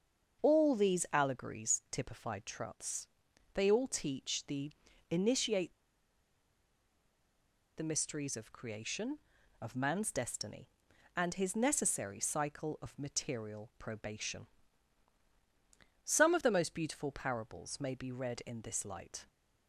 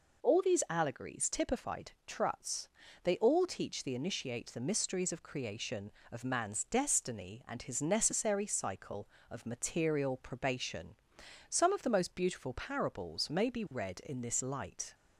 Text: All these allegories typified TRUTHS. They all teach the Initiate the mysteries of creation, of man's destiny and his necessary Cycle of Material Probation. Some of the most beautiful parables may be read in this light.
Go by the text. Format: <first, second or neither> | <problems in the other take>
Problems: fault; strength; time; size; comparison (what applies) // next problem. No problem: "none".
second | starts louder than the rest; until 1.4 s; 7 dB // pauses between "the" and "Initiate"; at 4.7 s; 0.40 s long // pauses between "Initiate" and "the"; strong; at 5.7 s; 2.0 s long